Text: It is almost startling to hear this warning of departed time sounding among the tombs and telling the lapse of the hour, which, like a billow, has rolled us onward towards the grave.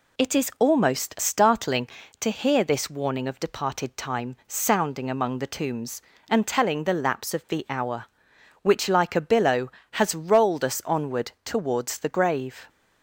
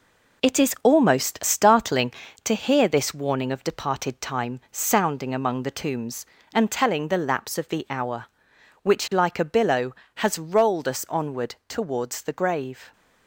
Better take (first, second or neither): first